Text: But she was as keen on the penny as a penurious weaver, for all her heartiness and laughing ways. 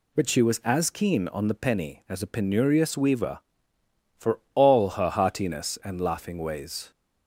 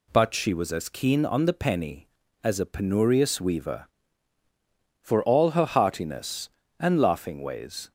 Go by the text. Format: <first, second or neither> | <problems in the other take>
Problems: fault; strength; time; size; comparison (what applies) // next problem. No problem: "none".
neither | none